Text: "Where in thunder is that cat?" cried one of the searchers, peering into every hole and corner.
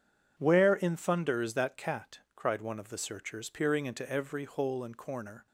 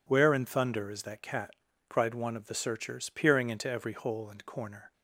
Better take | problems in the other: neither | none

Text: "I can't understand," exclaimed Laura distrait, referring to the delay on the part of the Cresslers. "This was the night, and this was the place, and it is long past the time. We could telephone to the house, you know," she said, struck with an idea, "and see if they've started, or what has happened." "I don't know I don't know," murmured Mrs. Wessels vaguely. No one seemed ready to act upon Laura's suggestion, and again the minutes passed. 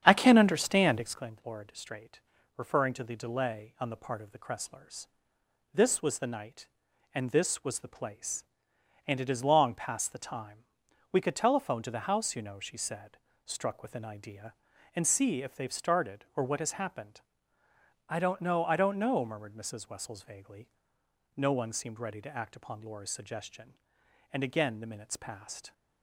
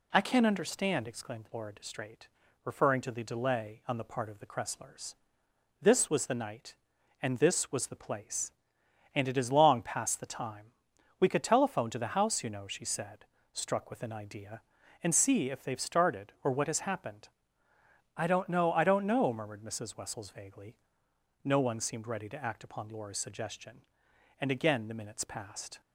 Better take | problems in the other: second | starts louder than the rest; strong; until 1.3 s; 9 dB

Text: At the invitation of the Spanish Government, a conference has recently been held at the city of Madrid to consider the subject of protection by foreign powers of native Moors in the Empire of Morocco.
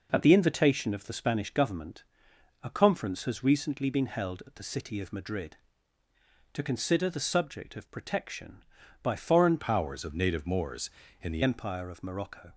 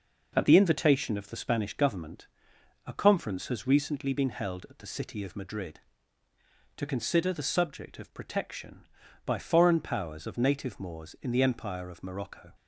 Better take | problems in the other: second | changes voice from "powers" to "the"; from 9.5 to 11.4 s; 1.9 s long

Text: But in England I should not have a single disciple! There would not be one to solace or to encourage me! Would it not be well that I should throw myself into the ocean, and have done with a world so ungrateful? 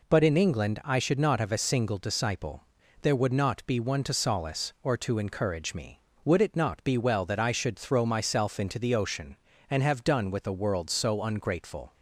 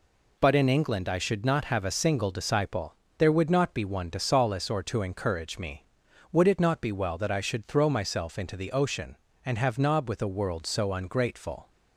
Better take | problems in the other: first | says "nob" for "done"; at 9.7 s

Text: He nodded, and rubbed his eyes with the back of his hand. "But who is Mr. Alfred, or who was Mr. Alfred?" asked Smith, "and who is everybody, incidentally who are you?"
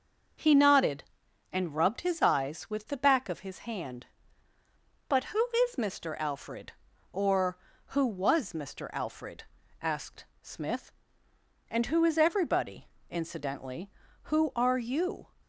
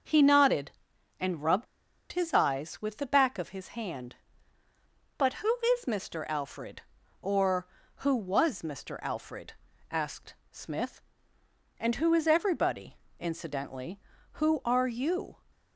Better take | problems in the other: first | starts louder than the rest; until 1.5 s; 6.5 dB; also in the first // pauses between "rubbed" and "his"; noticeable; at 1.6 s; 0.46 s long // pauses between "asked" and "Smith"; slight; at 10.3 s; 0.16 s long; slight in the first

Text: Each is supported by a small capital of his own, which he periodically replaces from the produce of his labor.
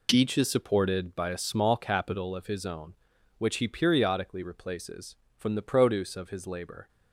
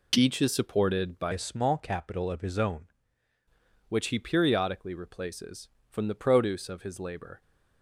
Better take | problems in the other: first | changes voice from "a" to "own"; from 1.3 to 2.8 s; 1.5 s long

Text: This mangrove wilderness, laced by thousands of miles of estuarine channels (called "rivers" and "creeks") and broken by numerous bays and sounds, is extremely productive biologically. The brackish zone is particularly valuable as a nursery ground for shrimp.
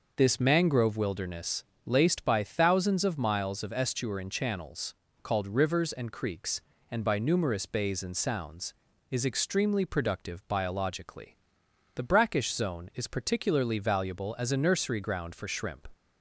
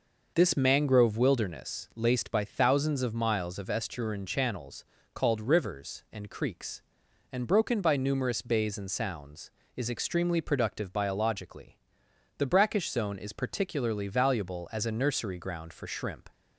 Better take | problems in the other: second | skips "broken"; at 7.0 s

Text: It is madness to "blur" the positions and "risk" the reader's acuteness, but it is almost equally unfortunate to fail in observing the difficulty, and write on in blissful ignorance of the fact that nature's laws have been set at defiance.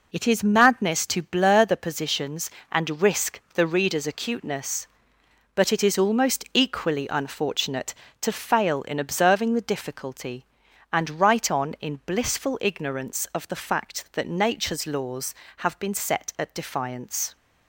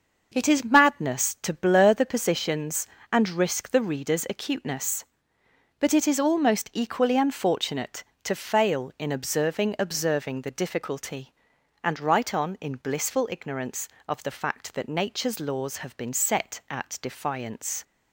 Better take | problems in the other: first | starts louder than the rest; until 1.3 s; 6 dB // says "observing" twice; at 9.7 s

